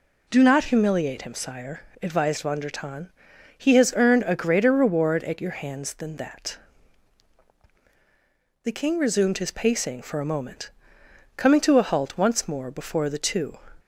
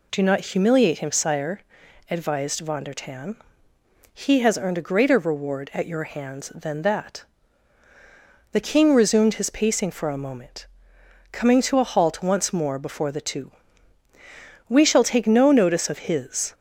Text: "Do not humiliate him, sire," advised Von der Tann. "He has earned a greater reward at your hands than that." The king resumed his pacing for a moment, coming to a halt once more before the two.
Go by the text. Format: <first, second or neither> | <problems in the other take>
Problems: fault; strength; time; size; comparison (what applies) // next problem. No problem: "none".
first | goes on to say "We shall take no notice of his"; strong; from 14.6 s on; 1.8 s long